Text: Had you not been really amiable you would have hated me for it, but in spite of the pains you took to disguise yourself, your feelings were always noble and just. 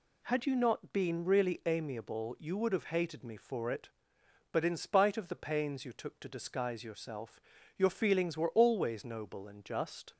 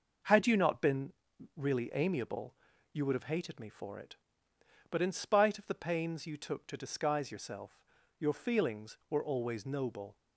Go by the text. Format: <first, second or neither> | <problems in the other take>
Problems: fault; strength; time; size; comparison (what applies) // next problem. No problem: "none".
first | pauses between "been" and "really"; at 1.1 s; 0.44 s long // pauses between "amiable" and "you"; at 2.5 s; 0.38 s long // stops before "and just"; at 10.1 s